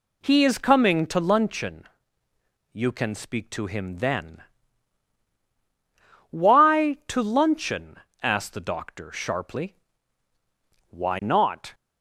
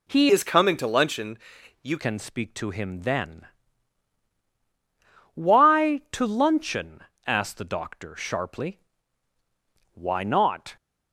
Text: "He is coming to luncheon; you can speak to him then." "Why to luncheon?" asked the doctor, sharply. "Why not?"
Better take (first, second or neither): first